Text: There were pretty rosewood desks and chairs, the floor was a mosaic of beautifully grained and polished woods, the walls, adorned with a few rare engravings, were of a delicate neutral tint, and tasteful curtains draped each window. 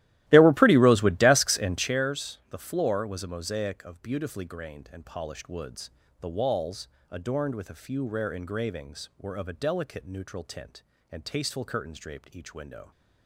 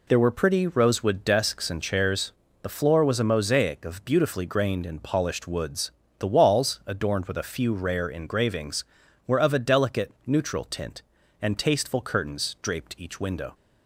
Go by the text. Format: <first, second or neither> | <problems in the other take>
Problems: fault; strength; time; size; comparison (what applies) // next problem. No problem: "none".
second | starts louder than the rest; strong; until 1.9 s; 15.5 dB